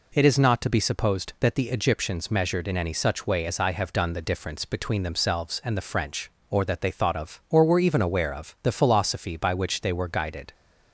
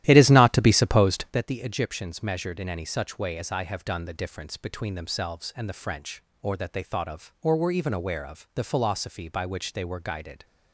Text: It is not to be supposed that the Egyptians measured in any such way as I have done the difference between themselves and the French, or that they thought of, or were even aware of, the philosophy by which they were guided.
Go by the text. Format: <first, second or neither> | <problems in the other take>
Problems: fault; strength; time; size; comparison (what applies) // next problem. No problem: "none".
first | starts louder than the rest; strong; until 1.3 s; 13 dB